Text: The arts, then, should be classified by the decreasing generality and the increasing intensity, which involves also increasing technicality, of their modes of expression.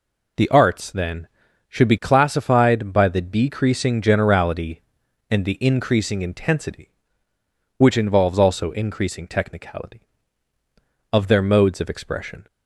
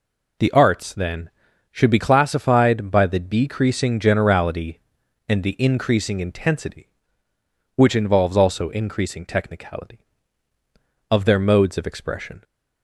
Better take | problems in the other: neither | none

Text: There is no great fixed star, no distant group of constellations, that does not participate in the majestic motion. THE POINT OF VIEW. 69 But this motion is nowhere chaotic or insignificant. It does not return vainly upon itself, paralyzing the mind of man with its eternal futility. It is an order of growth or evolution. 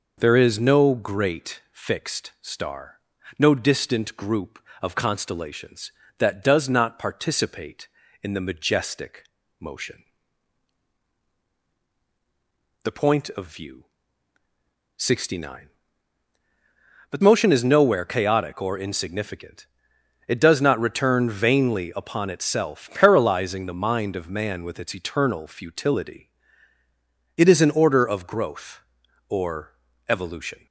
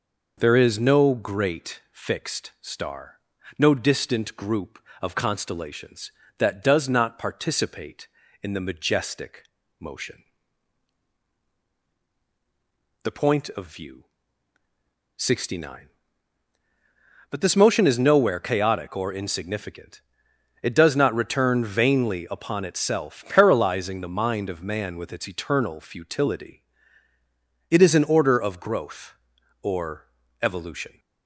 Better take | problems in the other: second | pauses between "majestic" and "motion"; at 9.2 s; 0.38 s long; also in the second // skips "this"; at 17.2 s // pauses between "or" and "evolution"; at 29.7 s; 0.38 s long; also in the second

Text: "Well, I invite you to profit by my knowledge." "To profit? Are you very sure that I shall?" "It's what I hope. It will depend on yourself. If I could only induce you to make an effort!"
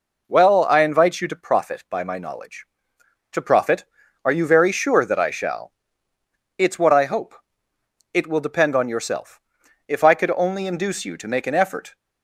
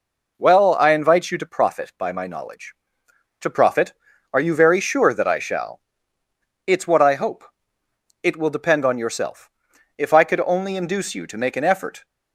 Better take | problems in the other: neither | none

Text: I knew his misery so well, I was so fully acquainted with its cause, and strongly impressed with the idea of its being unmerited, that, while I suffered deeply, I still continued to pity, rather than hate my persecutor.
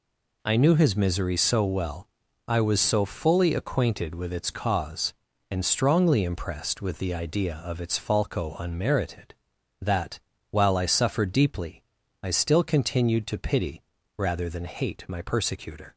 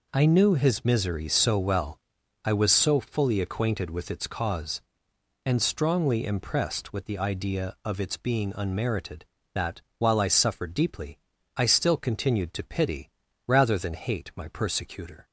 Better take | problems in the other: second | says "falco" for "being"; at 7.9 s

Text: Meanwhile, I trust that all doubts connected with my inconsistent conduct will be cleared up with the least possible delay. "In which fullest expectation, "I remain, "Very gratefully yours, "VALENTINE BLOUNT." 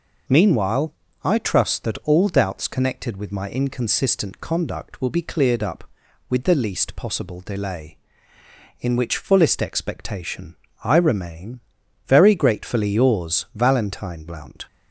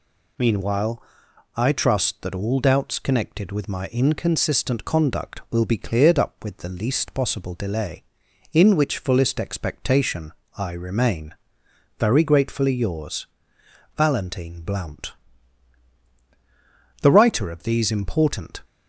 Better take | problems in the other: first | goes on to say "The writer of these important"; from 17.0 s on; 1.6 s long

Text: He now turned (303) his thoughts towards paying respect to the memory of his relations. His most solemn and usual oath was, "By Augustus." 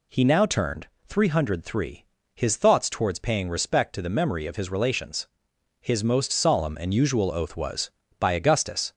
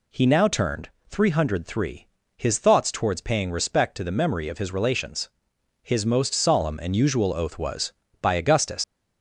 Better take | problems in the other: first | leaves "Augustus" unfinished; at 8.8 s; 110 ms

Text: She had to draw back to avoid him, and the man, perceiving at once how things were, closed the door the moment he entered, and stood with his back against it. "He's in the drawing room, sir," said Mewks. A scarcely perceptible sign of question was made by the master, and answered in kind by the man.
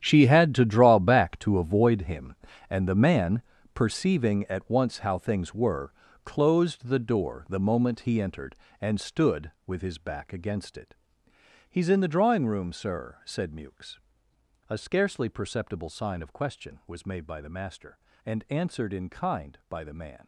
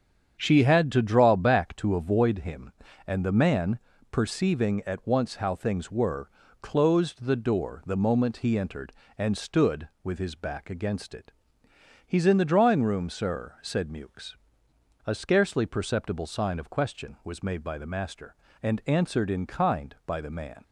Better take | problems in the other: second | gets quieter; strong; throughout; 14 dB // starts louder than the rest; strong; until 1.0 s; 9.5 dB; strong in the second

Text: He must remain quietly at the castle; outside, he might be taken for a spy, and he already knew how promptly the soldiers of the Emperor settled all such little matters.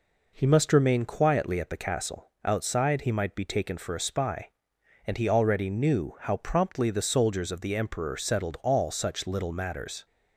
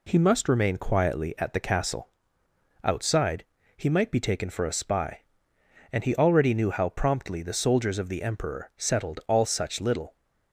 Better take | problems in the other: first | stops before "matters"; at 10.1 s

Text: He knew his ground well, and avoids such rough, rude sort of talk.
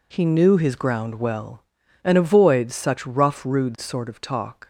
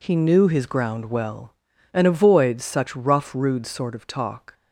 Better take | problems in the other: neither | none

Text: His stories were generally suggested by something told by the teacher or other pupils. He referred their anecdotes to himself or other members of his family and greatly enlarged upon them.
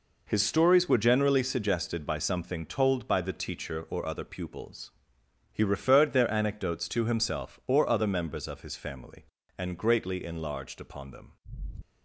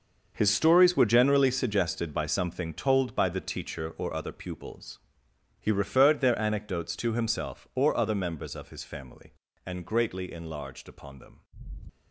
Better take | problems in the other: first | gets quieter; strong; throughout; 12 dB

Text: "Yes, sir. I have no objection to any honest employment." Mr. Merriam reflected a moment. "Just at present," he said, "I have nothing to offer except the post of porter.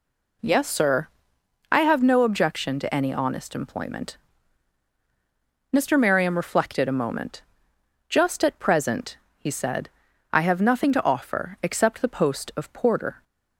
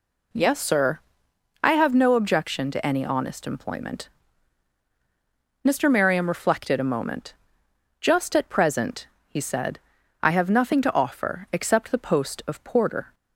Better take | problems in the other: neither | none

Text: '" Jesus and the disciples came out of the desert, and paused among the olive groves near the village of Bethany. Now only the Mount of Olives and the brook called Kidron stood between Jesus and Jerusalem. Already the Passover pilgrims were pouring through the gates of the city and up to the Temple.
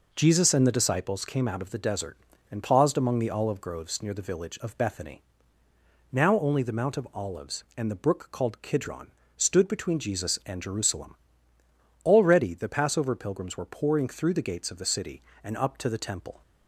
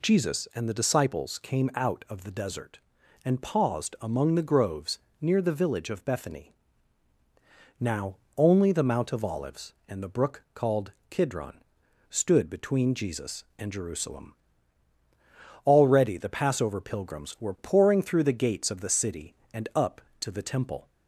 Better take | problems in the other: first | skips "olive"; at 4.4 s // pauses between "groves" and "near"; slight; at 4.9 s; 0.24 s long // pauses between "Now" and "only"; slight; at 8.1 s; 0.18 s long // pauses between "called" and "Kidron"; slight; at 10.9 s; 0.20 s long // pauses between "Kidron" and "stood"; noticeable; at 11.6 s; 0.48 s long; slight in the first

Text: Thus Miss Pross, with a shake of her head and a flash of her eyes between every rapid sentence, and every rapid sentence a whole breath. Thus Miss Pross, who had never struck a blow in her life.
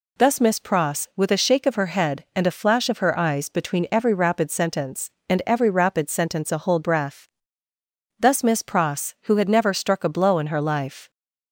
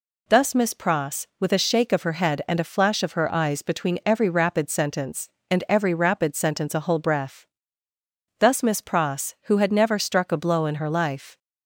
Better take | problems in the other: neither | none

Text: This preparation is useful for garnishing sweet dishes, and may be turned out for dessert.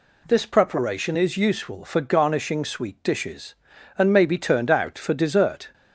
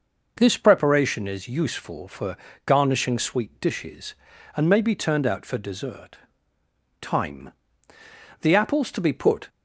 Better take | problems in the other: first | pauses between "for" and "garnishing"; slight; at 2.3 s; 0.30 s long // goes on to say "Time The apples to be put"; strong; from 7.0 s on; 2.4 s long

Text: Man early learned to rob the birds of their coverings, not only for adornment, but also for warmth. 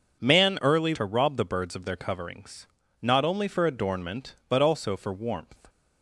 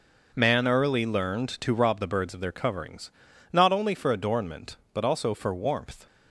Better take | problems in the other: second | skips "learned"; at 0.9 s

